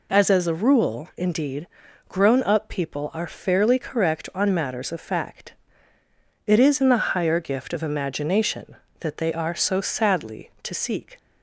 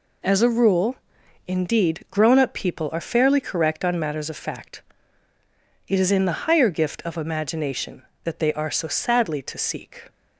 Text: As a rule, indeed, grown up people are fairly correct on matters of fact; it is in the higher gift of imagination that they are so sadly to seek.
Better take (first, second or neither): second